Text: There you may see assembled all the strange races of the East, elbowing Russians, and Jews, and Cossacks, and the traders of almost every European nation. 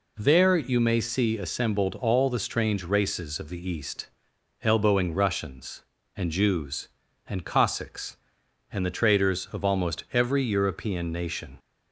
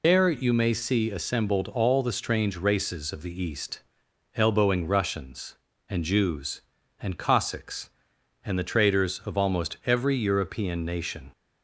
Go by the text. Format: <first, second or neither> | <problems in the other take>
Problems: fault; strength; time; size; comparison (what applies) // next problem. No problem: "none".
first | loses the start of "There"; at 0.0 s; 150 ms